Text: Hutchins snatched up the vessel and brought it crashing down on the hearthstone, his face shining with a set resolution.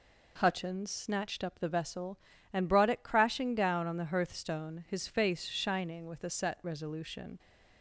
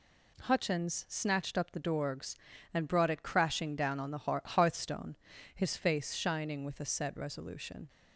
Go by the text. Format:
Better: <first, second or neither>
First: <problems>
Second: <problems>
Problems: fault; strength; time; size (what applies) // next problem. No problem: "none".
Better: first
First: none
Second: says "dorgs" for "vessel"; at 1.8 s